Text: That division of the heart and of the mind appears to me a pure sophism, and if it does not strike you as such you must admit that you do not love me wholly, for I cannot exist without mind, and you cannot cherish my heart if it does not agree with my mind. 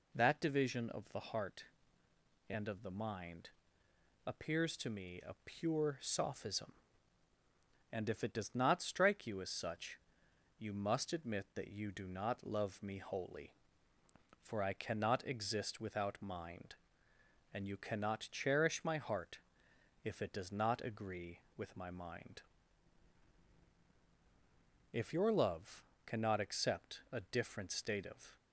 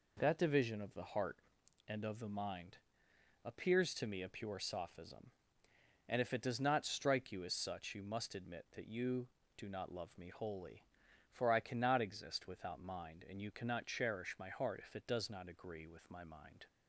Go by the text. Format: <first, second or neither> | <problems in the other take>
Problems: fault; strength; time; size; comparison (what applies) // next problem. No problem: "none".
second | pauses between "mind" and "appears"; noticeable; at 3.4 s; 0.76 s long; noticeable in the second // pauses between "such" and "you"; noticeable; at 9.9 s; 0.60 s long // pauses between "heart" and "if"; noticeable; at 19.3 s; 0.66 s long // goes on to say "If your love cannot accept a different state of"; strong; from 24.9 s on; 3.4 s long